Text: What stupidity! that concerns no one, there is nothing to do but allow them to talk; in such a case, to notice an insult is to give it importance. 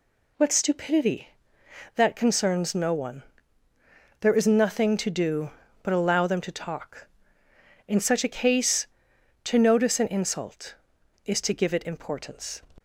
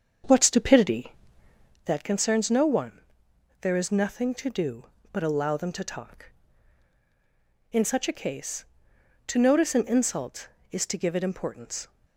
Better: first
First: none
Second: starts louder than the rest; strong; until 2.0 s; 7 dB

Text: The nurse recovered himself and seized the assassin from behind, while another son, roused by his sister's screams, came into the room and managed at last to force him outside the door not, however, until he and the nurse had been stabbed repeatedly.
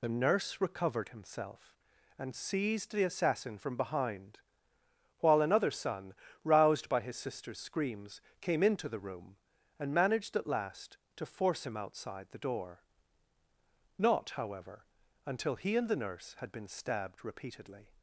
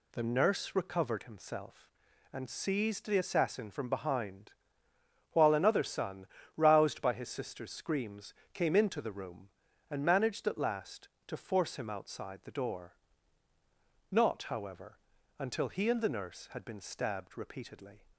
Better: second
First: loses the start of "The"; at 0.0 s; 45 ms // pauses between "door" and "not"; at 12.8 s; 1.1 s long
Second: pauses between "door" and "not"; at 12.9 s; 1.1 s long

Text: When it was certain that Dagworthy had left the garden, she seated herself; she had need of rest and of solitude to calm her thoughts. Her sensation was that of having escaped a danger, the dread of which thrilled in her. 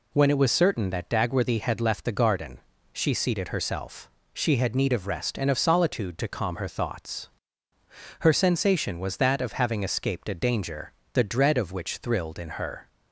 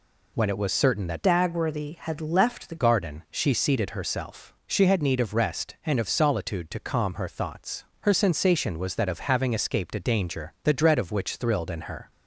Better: first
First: none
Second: changes voice from "Dagworthy" to "the"; from 1.2 to 2.7 s; 1.5 s long

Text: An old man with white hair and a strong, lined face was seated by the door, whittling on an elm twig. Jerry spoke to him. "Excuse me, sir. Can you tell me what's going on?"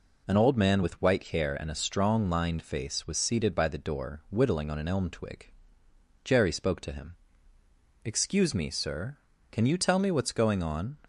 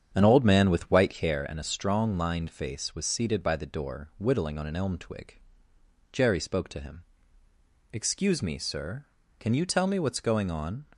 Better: first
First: none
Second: starts louder than the rest; strong; until 1.4 s; 8.5 dB

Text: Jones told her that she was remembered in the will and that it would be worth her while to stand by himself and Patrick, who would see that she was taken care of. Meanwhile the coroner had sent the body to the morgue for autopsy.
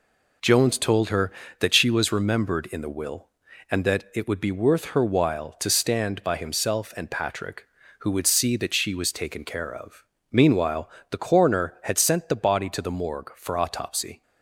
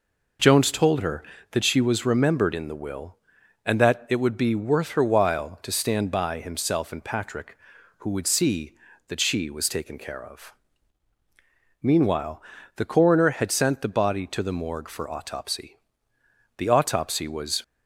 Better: first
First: pauses between "Meanwhile" and "the"; slight; at 10.8 s; 0.22 s long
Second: pauses between "Meanwhile" and "the"; slight; at 12.4 s; 0.34 s long // goes on to say "The autopsy was"; noticeable; from 16.5 s on; 1.0 s long

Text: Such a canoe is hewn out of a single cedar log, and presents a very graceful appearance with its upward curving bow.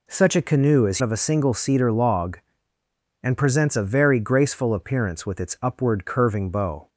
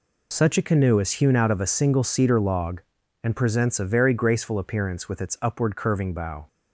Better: second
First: skips "hewn out"; at 1.0 s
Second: none

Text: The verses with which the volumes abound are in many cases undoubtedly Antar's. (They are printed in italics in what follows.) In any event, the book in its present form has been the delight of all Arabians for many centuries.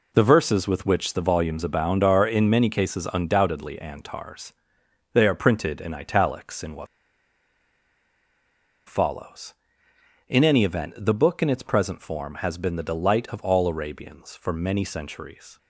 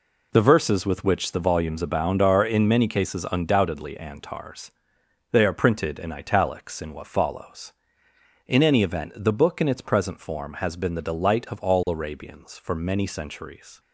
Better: second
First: pauses between "what" and "follows"; strong; at 6.8 s; 2.0 s long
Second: none

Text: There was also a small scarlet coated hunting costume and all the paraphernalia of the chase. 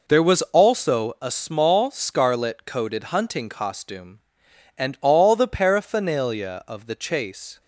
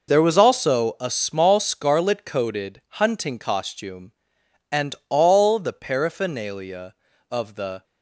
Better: first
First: none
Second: stops before "chase"; at 7.8 s

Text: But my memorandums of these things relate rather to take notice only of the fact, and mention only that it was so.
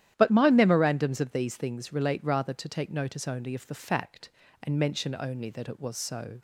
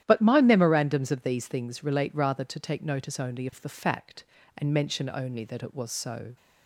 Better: neither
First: starts louder than the rest; strong; until 1.1 s; 11.5 dB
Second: starts louder than the rest; strong; until 1.0 s; 11.5 dB

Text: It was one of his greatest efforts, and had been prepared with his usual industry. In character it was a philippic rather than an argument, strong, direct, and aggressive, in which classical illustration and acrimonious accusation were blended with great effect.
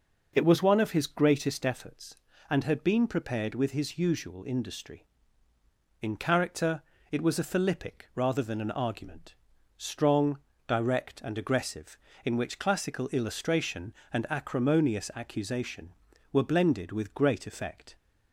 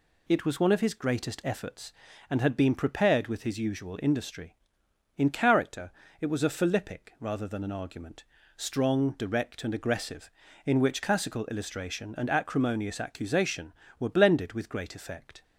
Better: neither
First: pauses between "character" and "it"; slight; at 6.8 s; 0.30 s long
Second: pauses between "character" and "it"; slight; at 5.9 s; 0.30 s long

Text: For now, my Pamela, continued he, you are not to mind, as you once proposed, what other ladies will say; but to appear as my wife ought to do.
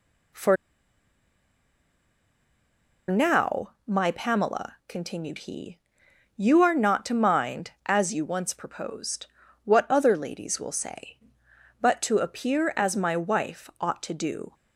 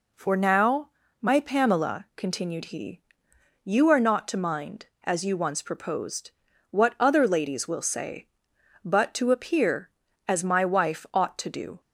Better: second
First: pauses between "For" and "now"; strong; at 0.5 s; 2.5 s long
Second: none

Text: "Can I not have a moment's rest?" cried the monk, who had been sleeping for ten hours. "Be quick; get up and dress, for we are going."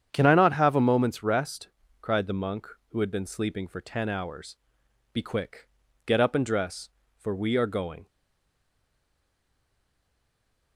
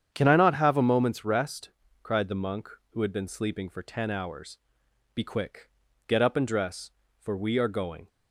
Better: second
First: starts louder than the rest; strong; until 1.1 s; 8.5 dB // stays silent after the last word; strong; from 8.0 s on; 2.7 s long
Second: starts louder than the rest; strong; until 1.1 s; 8.5 dB

